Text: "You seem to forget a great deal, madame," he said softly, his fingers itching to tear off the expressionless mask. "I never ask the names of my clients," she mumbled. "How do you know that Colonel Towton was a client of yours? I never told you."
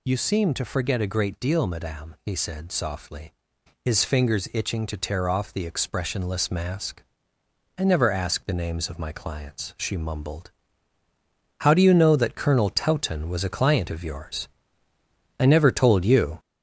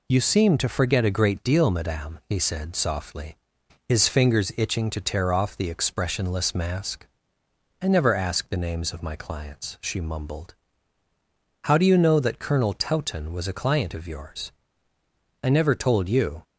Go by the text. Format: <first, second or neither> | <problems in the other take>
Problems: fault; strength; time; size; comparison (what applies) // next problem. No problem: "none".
second | gets louder; throughout; 3.5 dB